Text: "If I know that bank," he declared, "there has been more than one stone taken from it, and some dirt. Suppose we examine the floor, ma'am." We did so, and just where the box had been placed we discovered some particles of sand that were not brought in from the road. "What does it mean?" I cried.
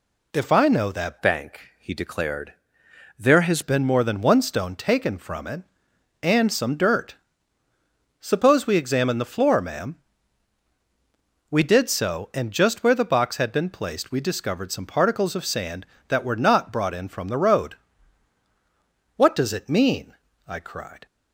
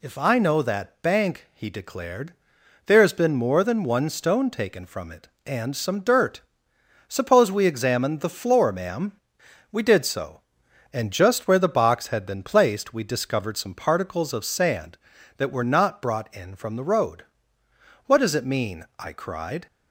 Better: second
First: changes voice from "bank" to "has"; from 1.2 to 3.6 s; 2.4 s long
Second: none

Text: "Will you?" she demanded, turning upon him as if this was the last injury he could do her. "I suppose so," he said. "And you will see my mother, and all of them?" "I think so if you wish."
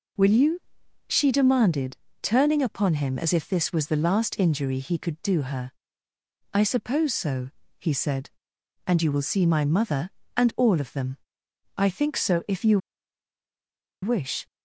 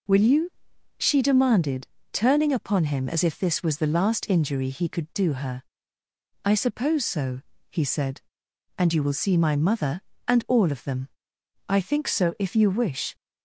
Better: second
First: pauses between "you" and "wish"; strong; at 12.7 s; 1.2 s long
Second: none

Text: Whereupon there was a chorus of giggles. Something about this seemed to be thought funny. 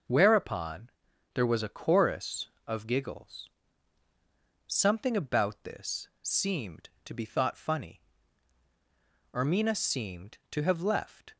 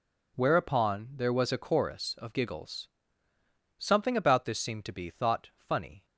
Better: second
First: starts louder than the rest; until 1.5 s; 6.5 dB // pauses between "Whereupon" and "there"; at 0.9 s; 0.44 s long // goes on to say "Ermina seemed to have left"; strong; from 9.3 s on; 2.0 s long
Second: none

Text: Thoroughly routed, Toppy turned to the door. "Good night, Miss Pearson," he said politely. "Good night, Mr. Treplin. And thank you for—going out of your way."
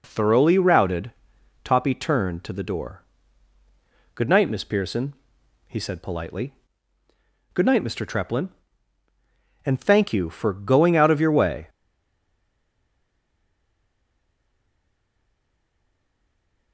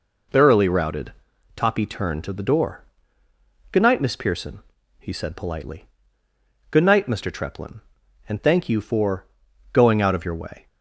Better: second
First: stays silent after the last word; strong; from 11.6 s on; 5.1 s long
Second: none

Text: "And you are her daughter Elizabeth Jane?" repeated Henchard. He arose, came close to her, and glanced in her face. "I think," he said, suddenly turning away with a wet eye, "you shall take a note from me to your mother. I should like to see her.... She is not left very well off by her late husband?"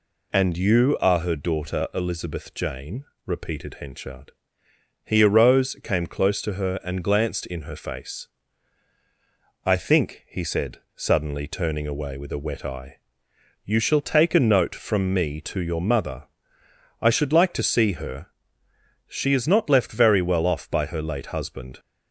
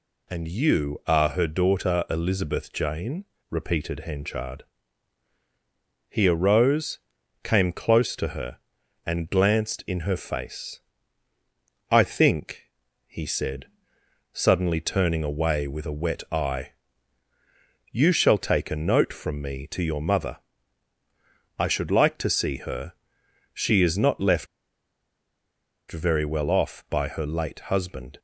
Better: first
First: none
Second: pauses between "left" and "very"; strong; at 24.4 s; 1.4 s long

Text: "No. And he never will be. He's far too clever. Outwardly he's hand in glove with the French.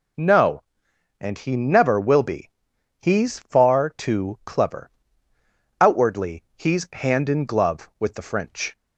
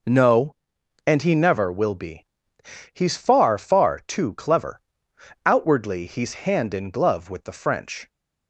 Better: first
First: none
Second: says "far" twice; at 3.5 s

